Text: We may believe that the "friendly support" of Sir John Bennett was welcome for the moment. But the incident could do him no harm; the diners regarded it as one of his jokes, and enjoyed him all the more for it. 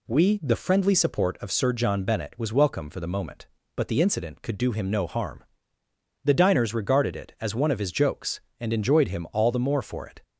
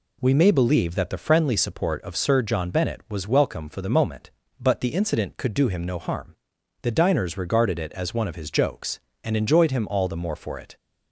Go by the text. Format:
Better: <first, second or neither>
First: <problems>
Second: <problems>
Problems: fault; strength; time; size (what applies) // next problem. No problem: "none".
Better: second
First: skips "may believe that"; at 0.4 s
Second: none